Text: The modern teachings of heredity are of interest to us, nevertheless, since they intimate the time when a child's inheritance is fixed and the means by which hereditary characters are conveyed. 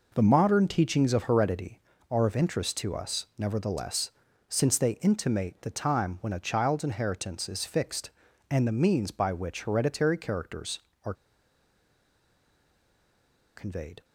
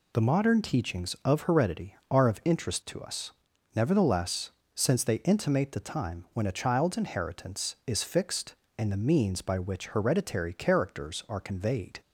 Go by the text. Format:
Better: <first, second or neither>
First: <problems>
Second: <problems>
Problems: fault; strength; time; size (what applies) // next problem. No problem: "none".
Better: second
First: pauses between "are" and "conveyed"; strong; at 11.1 s; 2.4 s long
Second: none